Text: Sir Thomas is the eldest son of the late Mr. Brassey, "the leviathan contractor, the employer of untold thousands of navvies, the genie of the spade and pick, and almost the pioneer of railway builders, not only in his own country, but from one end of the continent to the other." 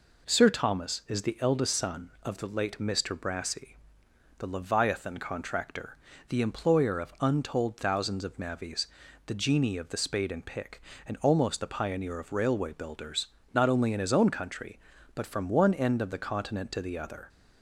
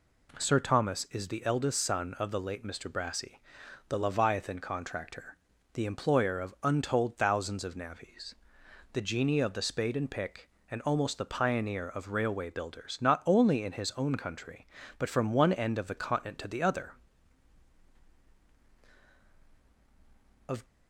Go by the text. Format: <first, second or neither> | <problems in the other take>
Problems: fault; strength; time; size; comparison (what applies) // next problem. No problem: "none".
first | goes on to say "Of"; slight; from 20.4 s on; 0.16 s long